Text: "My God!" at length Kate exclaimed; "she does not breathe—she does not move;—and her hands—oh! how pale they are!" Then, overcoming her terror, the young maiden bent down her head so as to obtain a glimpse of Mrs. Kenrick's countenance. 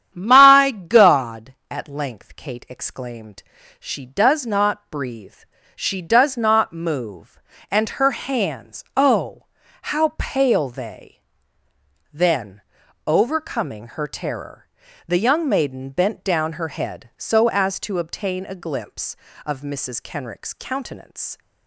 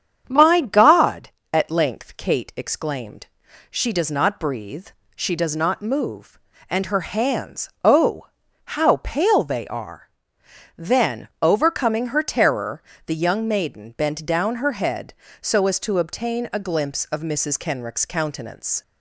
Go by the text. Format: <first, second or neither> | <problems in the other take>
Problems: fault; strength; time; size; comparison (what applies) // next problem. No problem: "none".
second | starts louder than the rest; strong; until 1.1 s; 9.5 dB; strong in the second // skips "are"; at 11.6 s